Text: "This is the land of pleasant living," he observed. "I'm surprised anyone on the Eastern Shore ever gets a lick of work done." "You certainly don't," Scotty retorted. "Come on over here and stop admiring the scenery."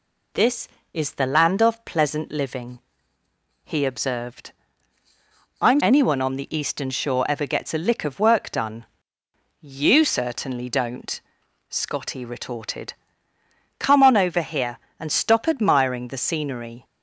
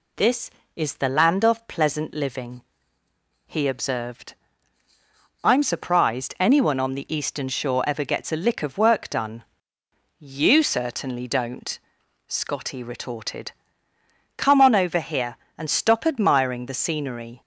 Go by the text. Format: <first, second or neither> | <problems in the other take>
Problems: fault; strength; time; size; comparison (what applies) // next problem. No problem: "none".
second | skips "surprised"; at 5.7 s